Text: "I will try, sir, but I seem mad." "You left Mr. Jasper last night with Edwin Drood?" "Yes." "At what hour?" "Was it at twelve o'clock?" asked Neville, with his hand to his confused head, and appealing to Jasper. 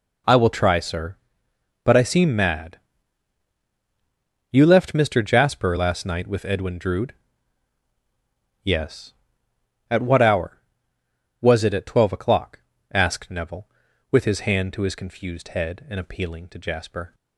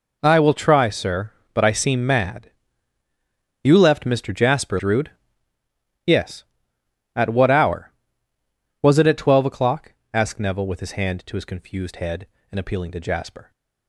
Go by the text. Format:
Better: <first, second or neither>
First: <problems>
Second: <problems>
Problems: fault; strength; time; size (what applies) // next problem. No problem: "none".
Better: first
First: none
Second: skips "last night with Edwin"; at 4.7 s